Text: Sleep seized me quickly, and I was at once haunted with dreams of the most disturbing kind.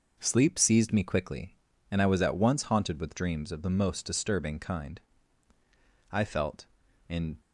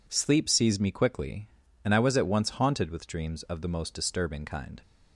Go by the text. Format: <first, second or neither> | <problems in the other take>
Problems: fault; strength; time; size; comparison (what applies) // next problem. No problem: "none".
second | goes on to say "I felt in"; noticeable; from 6.1 s on; 1.2 s long